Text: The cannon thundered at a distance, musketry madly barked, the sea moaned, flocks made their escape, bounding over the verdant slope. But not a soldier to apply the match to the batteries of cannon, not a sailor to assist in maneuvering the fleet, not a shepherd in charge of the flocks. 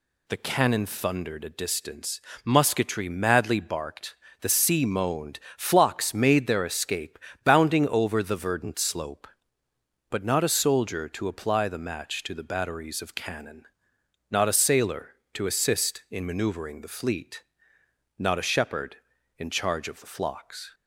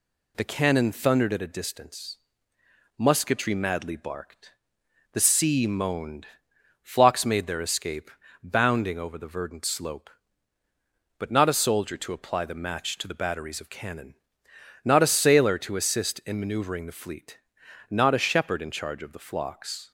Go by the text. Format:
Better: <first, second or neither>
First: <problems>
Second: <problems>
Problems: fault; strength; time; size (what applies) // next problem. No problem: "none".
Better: second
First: skips "at"; at 1.4 s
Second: none